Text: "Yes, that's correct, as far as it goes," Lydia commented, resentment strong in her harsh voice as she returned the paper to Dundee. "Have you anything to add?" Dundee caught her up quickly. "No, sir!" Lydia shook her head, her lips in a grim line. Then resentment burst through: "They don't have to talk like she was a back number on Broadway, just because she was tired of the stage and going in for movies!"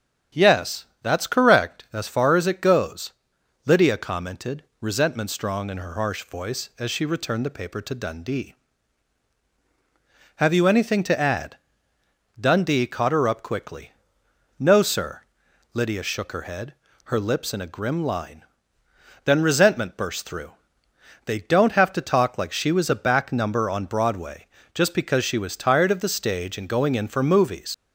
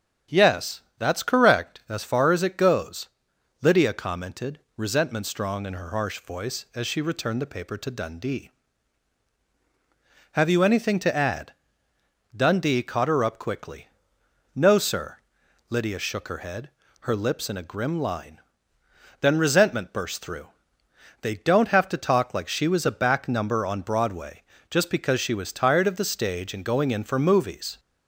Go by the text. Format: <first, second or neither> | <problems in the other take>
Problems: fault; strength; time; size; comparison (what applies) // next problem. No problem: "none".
second | starts louder than the rest; strong; until 1.5 s; 8 dB; strong in the second // leaves "movies" unfinished; at 27.7 s; 90 ms